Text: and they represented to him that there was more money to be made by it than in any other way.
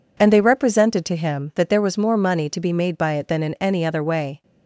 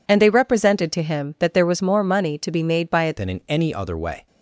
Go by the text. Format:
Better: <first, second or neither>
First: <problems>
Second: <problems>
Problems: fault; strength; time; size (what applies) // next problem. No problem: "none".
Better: first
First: none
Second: changes voice at "than"; from 3.1 s on; 1.1 s long